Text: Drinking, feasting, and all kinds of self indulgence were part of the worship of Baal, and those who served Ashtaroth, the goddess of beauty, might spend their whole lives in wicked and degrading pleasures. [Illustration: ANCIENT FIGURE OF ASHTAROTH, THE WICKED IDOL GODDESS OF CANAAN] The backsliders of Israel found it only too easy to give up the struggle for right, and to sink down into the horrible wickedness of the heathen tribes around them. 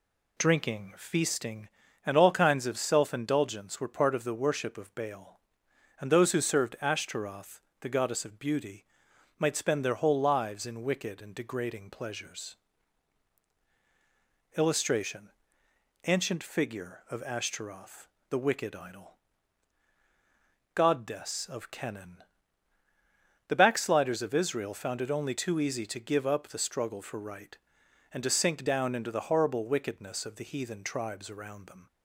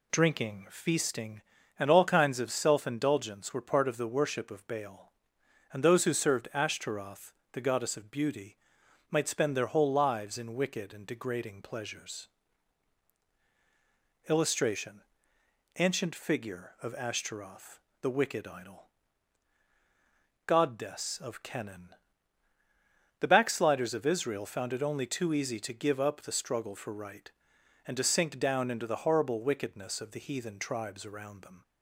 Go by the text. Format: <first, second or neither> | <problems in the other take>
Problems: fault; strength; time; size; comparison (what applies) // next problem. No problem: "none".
neither | pauses between "IDOL" and "GODDESS"; strong; the same in both // pauses between "CANAAN" and "The"; strong; the same in both